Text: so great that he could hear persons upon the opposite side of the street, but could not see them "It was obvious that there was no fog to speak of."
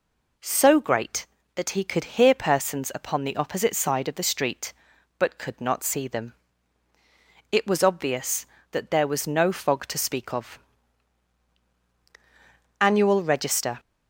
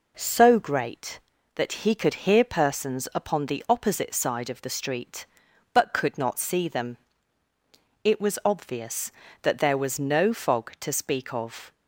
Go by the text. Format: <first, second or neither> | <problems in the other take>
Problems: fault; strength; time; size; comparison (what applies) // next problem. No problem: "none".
second | pauses between "them" and "It"; at 6.3 s; 1.1 s long; also in the second // goes on to say "Annual Register"; noticeable; from 12.7 s on; 1.0 s long